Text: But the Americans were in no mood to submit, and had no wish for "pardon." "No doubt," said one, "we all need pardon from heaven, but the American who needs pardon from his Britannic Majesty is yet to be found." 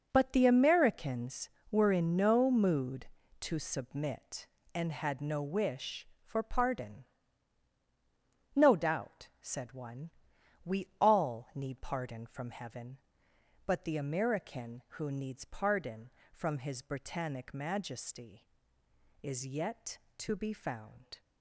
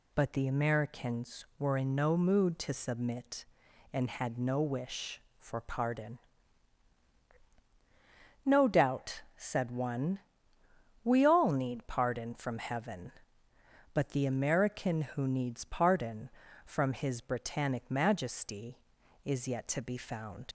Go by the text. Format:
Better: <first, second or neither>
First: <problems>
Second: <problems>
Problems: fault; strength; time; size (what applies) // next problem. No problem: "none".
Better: first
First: none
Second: leaves "found" unfinished; at 20.4 s; 85 ms